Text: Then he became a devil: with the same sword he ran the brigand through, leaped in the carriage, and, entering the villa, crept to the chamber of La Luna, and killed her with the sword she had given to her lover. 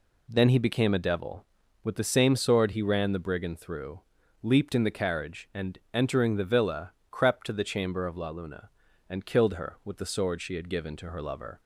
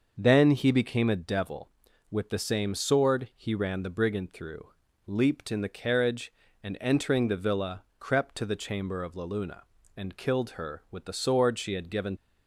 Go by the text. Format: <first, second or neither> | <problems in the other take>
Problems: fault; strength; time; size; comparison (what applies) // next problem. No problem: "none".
first | starts louder than the rest; noticeable; until 1.1 s; 6 dB // stops before "to her lover"; at 12.1 s